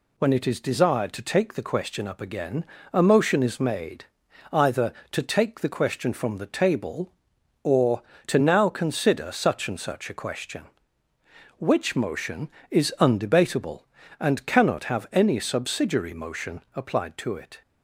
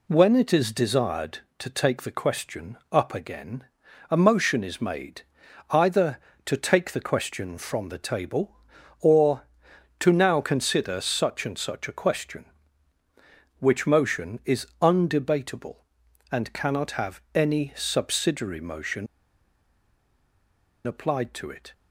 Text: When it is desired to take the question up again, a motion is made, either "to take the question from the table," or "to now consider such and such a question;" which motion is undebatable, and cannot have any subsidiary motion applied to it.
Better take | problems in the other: first | pauses between "question" and "up"; slight; at 2.7 s; 0.16 s long // pauses between "is" and "undebatable"; slight; at 14.6 s; 0.16 s long // pauses between "motion" and "applied"; strong; at 19.0 s; 1.8 s long

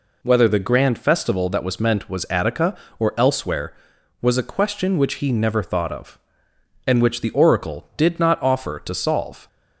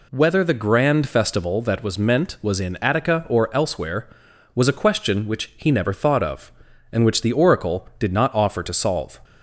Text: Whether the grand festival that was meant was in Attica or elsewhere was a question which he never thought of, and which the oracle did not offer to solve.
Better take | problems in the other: second | skips "in"; at 2.2 s

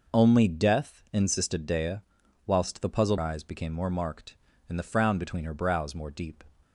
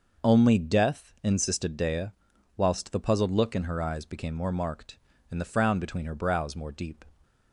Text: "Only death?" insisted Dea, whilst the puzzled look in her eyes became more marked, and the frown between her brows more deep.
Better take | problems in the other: second | skips "look in her"; at 3.1 s

